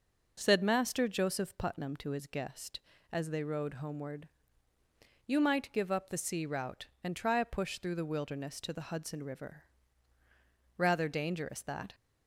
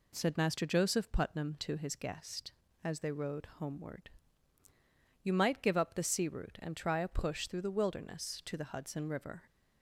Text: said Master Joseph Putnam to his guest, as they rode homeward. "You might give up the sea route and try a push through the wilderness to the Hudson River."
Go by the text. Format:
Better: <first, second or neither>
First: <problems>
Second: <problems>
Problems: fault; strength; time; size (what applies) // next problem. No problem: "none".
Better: second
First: goes on to say "Rather dangerous that"; noticeable; from 10.7 s on; 1.1 s long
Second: none